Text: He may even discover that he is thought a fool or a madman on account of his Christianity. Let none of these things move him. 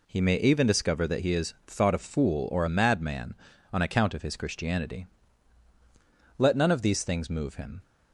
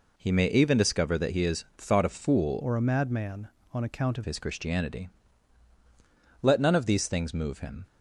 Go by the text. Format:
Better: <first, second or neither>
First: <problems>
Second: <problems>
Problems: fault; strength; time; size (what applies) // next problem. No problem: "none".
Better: first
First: none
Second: changes voice from "or" to "of"; from 2.6 to 4.2 s; 1.6 s long